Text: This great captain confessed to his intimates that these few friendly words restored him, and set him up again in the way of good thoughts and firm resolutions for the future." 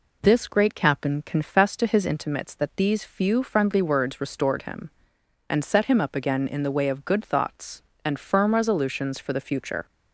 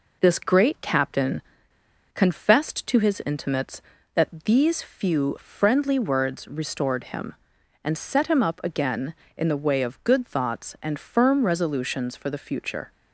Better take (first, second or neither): first